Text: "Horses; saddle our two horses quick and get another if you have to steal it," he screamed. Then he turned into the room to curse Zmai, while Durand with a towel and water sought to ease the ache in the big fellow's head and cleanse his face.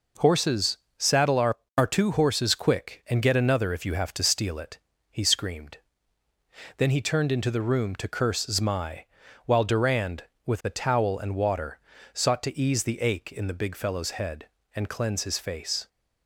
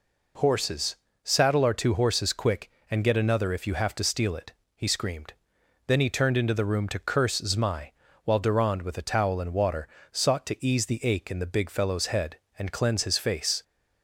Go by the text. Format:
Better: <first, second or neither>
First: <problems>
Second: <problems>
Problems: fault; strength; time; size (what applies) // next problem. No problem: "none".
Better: second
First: says "our" twice; at 1.7 s // pauses between "water" and "sought"; slight; at 11.7 s; 0.32 s long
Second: pauses between "water" and "sought"; slight; at 9.8 s; 0.24 s long